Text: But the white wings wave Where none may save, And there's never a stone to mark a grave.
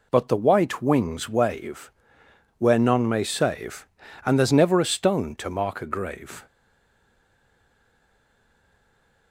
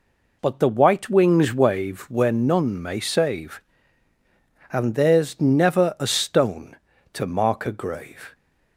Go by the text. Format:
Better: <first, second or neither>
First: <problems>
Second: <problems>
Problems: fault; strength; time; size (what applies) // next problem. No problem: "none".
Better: second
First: pauses between "wave" and "Where"; noticeable; at 1.9 s; 0.66 s long // stays silent after the last word; strong; from 6.4 s on; 2.9 s long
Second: none